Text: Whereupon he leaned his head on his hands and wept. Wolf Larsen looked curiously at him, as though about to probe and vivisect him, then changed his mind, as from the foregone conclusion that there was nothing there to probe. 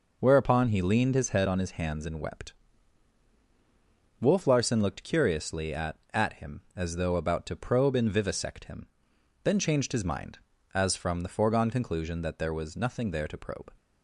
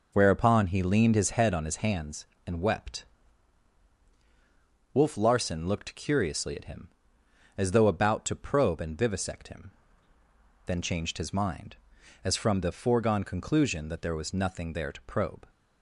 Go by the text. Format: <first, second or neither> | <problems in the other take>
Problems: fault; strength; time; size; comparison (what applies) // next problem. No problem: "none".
second | says "at" twice; at 6.1 s